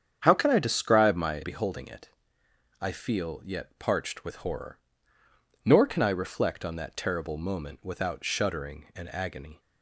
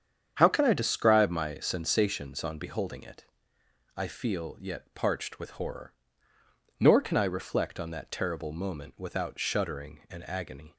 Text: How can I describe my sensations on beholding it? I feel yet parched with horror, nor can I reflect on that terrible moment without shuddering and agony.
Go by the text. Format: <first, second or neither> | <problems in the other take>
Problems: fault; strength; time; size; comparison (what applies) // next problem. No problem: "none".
second | starts louder than the rest; strong; until 1.2 s; 8 dB; strong in the second // skips "sensations on"; at 1.4 s